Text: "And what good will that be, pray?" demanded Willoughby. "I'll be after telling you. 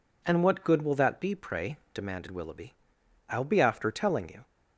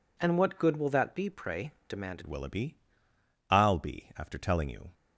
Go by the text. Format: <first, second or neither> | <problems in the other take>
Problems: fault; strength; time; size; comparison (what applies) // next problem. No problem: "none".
first | changes voice at "Willoughby"; from 2.2 s on; 2.6 s long